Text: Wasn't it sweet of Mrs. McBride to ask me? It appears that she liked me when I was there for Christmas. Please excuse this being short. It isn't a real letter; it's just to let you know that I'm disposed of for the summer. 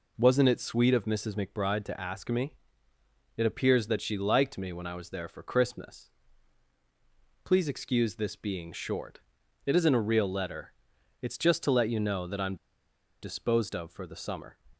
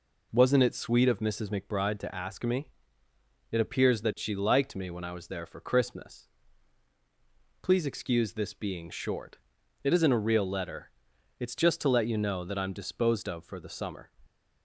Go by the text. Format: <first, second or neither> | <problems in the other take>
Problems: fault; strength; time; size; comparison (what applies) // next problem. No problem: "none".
second | pauses between "I'm" and "disposed"; noticeable; at 12.5 s; 0.67 s long